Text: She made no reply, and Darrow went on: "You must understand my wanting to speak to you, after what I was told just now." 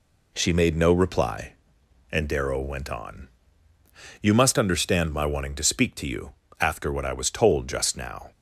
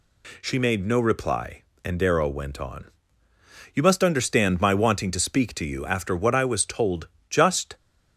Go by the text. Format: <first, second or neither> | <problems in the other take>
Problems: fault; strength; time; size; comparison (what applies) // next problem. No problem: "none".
first | pauses between "told" and "just"; slight; at 7.0 s; 0.24 s long // stops before "now"; at 7.7 s